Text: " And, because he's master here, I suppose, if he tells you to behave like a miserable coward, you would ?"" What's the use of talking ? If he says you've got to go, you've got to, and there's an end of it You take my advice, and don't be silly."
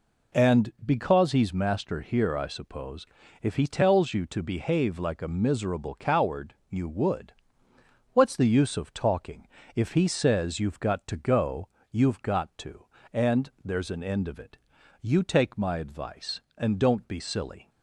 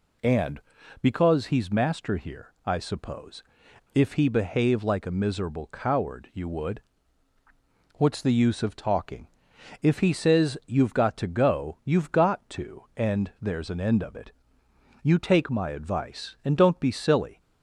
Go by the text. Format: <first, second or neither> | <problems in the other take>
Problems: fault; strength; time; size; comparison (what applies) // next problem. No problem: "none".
first | skips "tells you to"; at 4.2 s // pauses between "it" and "You"; noticeable; at 14.3 s; 0.70 s long; also in the first